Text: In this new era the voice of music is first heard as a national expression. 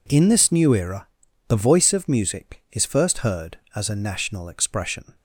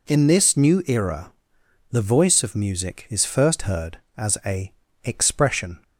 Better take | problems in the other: first | pauses between "era" and "the"; noticeable; at 1.3 s; 0.60 s long; also in the first // skips "national"; at 4.8 s

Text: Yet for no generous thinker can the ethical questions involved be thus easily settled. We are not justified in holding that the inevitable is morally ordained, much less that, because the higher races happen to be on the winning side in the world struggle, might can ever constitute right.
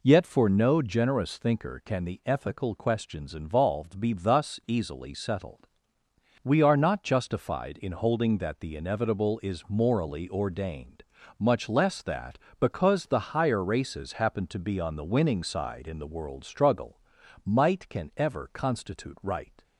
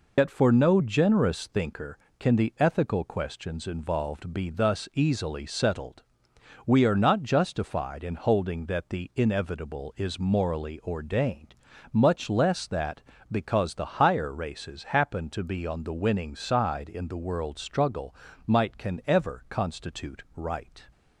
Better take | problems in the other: first | loses the start of "Yet"; at 0.1 s; 95 ms

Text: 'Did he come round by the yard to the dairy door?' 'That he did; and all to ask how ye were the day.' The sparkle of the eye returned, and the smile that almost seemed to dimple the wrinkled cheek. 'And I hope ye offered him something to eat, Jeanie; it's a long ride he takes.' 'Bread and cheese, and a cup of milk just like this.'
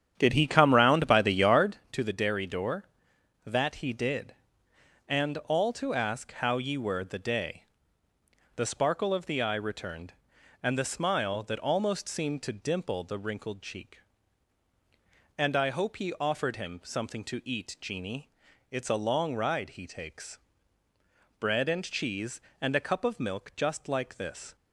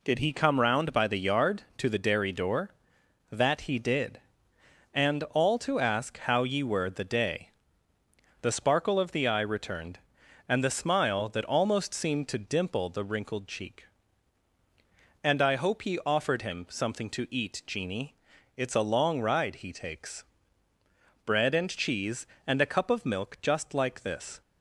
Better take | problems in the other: second | starts louder than the rest; strong; until 1.8 s; 9 dB

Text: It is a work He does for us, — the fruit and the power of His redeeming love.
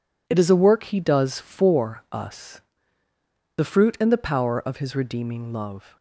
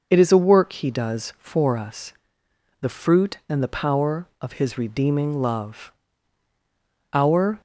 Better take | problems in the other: first | goes on to say "Our"; slight; from 7.1 s on; 0.48 s long

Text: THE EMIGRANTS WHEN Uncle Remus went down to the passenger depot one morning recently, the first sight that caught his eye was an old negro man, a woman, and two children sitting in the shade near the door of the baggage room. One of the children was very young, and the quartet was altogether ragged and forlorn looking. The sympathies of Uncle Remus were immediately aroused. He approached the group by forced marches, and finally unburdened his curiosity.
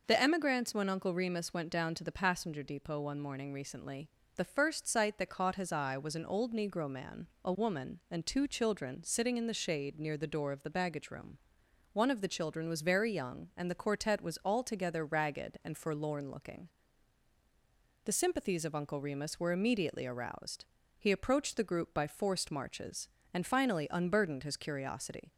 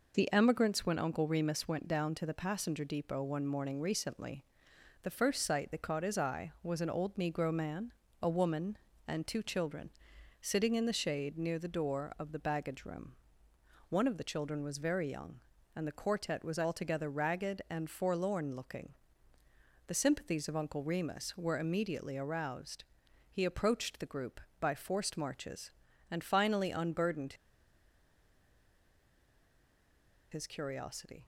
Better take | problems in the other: first | pauses between "children" and "sitting"; noticeable; at 9.8 s; 0.50 s long // pauses between "unburdened" and "his"; strong; at 27.3 s; 2.9 s long

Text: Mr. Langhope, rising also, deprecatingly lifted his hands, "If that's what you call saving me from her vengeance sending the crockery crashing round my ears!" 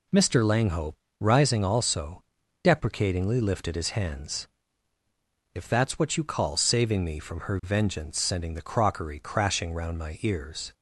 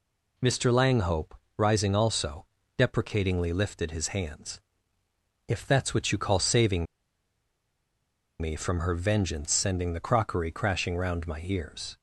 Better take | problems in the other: first | pauses between "saving" and "me"; strong; at 6.8 s; 1.5 s long

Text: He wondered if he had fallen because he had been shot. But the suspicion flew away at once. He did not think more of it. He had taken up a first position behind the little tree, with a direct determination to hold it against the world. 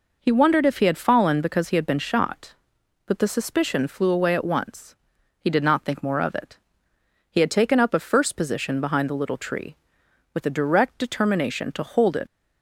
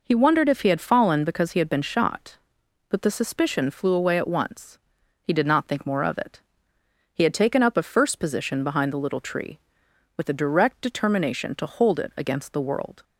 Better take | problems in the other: second | stops before "against the world"; at 12.2 s

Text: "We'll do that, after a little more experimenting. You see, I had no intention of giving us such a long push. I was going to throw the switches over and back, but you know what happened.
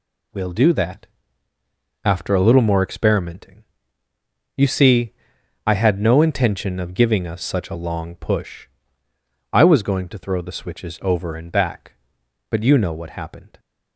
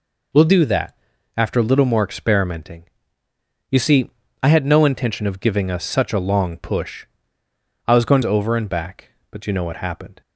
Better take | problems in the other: first | skips "to throw the switches"; at 8.2 s

